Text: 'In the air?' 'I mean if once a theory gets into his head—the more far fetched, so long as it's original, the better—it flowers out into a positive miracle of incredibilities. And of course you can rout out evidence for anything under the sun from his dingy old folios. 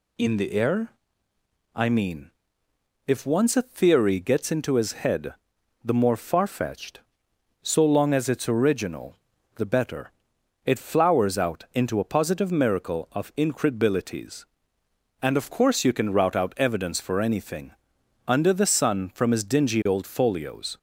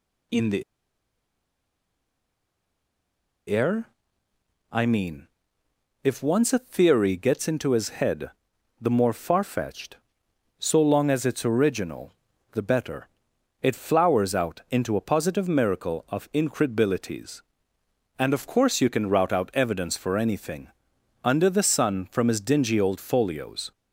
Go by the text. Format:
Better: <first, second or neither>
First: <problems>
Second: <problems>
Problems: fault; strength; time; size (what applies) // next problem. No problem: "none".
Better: first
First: pauses between "mean" and "if"; noticeable; at 2.2 s; 0.76 s long // pauses between "anything" and "under"; noticeable; at 17.7 s; 0.56 s long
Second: pauses between "the" and "air"; strong; at 0.6 s; 2.8 s long // pauses between "mean" and "if"; noticeable; at 5.2 s; 0.76 s long // pauses between "anything" and "under"; noticeable; at 20.6 s; 0.56 s long